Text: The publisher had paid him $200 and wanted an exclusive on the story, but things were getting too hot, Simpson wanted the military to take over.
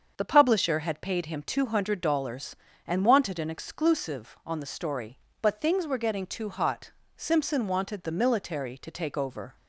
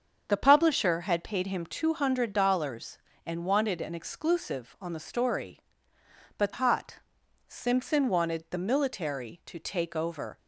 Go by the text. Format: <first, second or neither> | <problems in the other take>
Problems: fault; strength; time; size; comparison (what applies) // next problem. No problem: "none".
first | starts louder than the rest; until 1.2 s; 7 dB; also in the first // skips "things were getting too"; at 6.5 s